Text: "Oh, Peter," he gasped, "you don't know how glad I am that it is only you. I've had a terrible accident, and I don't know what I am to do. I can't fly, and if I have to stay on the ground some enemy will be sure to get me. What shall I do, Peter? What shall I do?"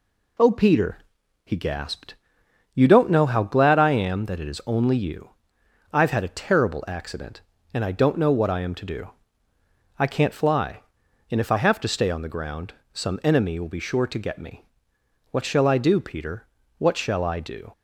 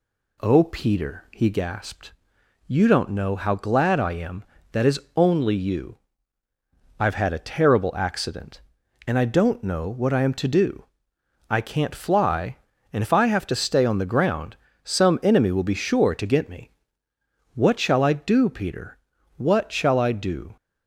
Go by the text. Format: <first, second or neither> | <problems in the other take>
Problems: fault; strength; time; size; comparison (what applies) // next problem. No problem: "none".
first | skips "it"; at 4.8 s // pauses between "is" and "only"; slight; at 4.9 s; 0.16 s long // pauses between "ground" and "some"; slight; at 14.5 s; 0.28 s long; slight in the first